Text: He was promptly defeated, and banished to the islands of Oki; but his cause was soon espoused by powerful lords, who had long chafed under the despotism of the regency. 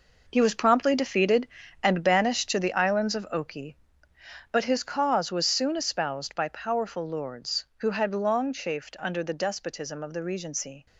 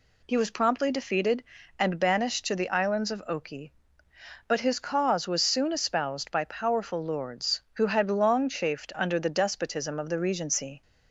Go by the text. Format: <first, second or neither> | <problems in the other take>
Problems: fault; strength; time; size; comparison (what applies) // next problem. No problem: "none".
second | gets quieter; strong; throughout; 9.5 dB